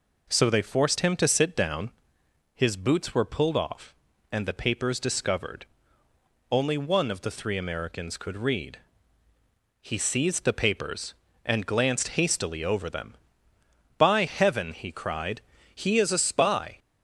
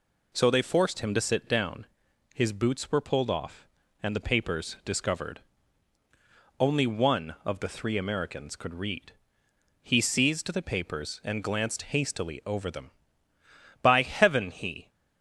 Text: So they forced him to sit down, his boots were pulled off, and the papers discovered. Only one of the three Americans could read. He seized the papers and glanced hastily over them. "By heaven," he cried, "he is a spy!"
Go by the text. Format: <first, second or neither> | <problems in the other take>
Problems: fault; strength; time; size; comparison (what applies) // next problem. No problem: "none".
first | stops before "cried he is a spy"; at 14.8 s